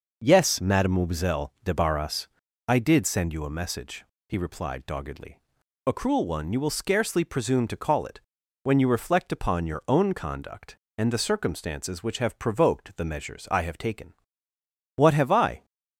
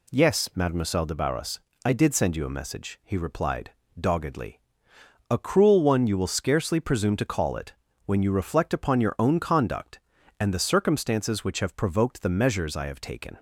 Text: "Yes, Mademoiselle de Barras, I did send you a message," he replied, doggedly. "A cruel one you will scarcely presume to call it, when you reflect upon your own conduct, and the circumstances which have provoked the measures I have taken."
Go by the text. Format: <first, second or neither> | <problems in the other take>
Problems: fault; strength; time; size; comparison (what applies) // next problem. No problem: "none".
second | goes on to say "What have I"; noticeable; from 14.9 s on; 0.70 s long